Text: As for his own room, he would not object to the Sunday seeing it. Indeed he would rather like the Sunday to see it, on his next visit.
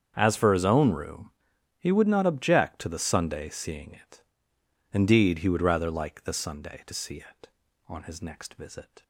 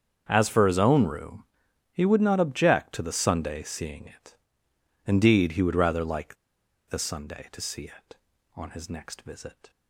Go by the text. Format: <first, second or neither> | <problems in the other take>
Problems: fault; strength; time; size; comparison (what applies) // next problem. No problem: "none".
first | starts louder than the rest; strong; until 1.2 s; 7.5 dB; strong in the first // pauses between "like" and "the"; noticeable; at 6.3 s; 0.54 s long